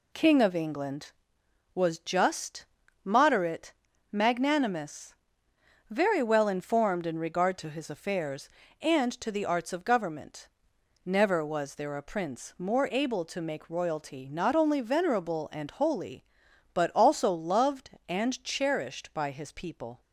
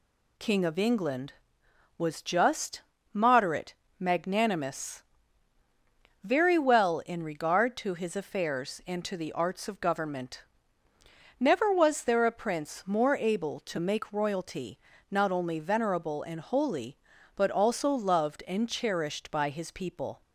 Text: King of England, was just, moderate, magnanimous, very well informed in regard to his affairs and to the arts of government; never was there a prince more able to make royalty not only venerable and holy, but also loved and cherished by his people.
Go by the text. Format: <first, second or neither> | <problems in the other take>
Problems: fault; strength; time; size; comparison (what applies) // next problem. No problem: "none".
first | skips "informed"; at 7.0 s // pauses between "royalty" and "not"; slight; at 14.7 s; 0.32 s long